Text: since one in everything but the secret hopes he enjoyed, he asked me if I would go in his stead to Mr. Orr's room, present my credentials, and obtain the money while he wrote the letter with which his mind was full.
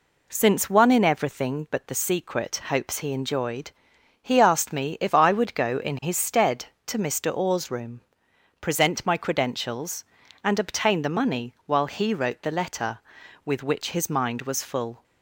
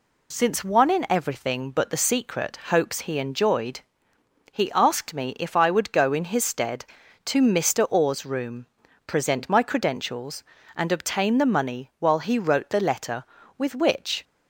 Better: first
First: none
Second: stops before "his mind was full"; at 14.2 s

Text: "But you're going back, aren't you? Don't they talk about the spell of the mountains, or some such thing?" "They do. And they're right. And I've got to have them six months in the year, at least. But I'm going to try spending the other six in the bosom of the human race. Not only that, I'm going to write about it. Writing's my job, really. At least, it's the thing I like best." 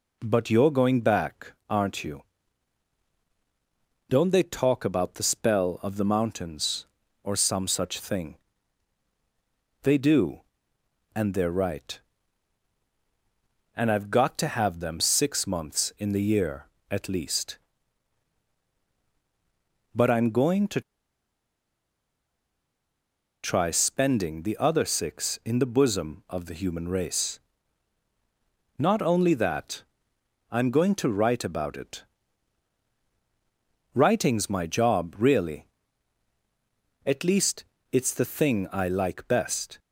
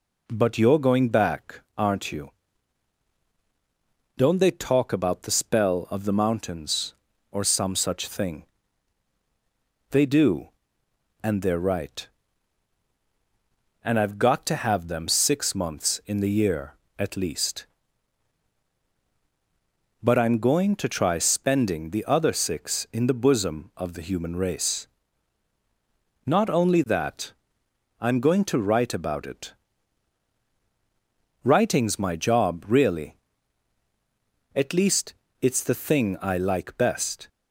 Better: second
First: pauses between "to" and "try"; strong; at 20.8 s; 2.6 s long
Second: none

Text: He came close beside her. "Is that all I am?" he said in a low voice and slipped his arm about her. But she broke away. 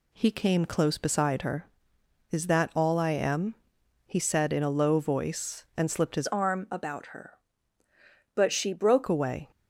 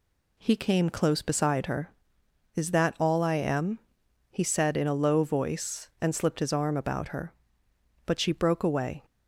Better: second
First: changes voice from "arm" to "broke"; from 6.2 to 9.0 s; 2.8 s long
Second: none

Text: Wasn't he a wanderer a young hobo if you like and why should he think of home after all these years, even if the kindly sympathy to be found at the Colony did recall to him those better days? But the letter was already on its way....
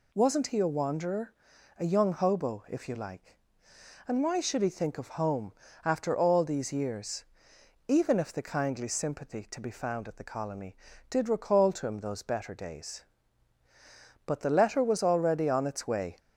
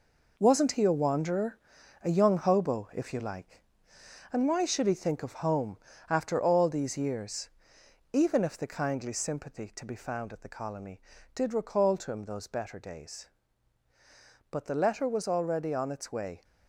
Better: first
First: pauses between "wanderer" and "a"; at 1.3 s; 0.44 s long // pauses between "home" and "after"; slight; at 5.5 s; 0.32 s long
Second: gets quieter; strong; throughout; 7 dB // pauses between "wanderer" and "a"; at 1.5 s; 0.44 s long // pauses between "home" and "after"; slight; at 5.7 s; 0.32 s long

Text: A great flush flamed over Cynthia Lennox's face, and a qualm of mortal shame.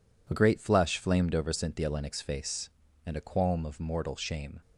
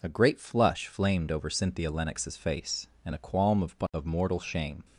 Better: first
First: none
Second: says "of" twice; at 3.9 s

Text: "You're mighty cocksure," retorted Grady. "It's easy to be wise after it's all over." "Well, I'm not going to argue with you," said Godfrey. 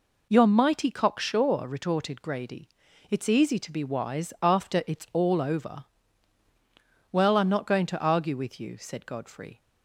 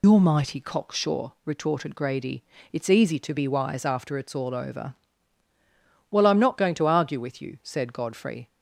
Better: first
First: none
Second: loses the start of "You're"; at 0.0 s; 80 ms

